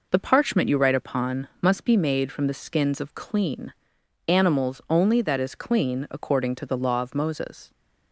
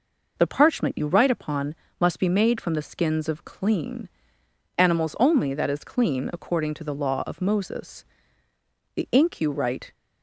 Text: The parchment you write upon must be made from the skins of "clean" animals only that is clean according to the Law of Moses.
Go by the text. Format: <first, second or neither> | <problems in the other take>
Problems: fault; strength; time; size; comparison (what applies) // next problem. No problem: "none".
first | pauses between "upon" and "must"; slight; at 1.7 s; 0.26 s long // pauses between "clean" and "animals"; noticeable; at 4.1 s; 0.66 s long; noticeable in the first // goes on to say "The ink you write"; noticeable; from 8.9 s on; 0.98 s long